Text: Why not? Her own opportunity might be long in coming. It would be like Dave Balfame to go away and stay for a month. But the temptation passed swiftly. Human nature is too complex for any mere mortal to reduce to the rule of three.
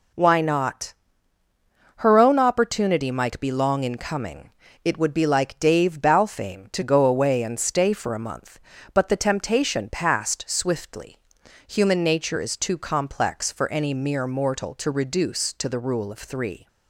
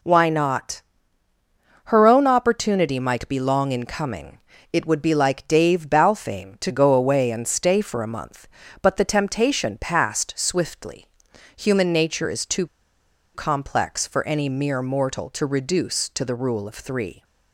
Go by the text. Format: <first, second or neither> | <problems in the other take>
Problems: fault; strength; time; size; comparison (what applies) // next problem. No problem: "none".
first | pauses between "too" and "complex"; noticeable; at 12.6 s; 0.68 s long